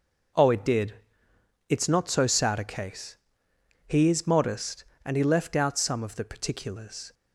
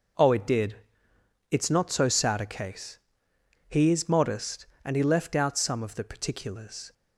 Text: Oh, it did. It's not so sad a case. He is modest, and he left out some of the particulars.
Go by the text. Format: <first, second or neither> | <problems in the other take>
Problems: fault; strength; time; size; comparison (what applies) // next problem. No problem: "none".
neither | none